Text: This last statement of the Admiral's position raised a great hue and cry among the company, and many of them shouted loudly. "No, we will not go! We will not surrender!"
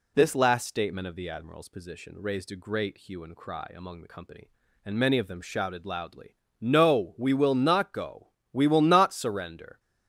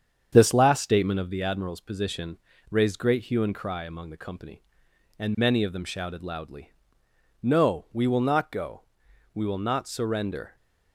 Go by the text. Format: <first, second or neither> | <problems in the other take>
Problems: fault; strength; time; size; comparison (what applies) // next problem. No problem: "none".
first | starts louder than the rest; strong; until 1.3 s; 8 dB // pauses between "position" and "raised"; slight; at 2.3 s; 0.34 s long // skips "a"; at 2.9 s